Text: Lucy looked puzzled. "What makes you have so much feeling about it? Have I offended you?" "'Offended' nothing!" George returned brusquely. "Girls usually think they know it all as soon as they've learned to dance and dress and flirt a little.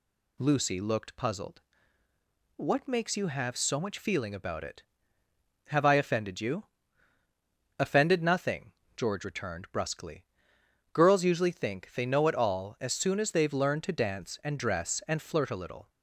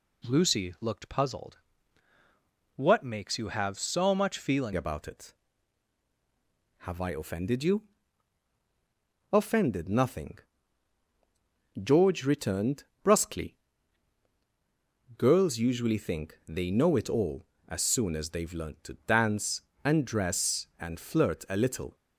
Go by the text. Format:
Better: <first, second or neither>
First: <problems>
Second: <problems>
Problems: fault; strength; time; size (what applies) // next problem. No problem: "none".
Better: first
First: none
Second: changes voice at "about"; from 4.7 s on; 17.2 s long // pauses between "returned" and "brusquely"; slight; at 12.8 s; 0.18 s long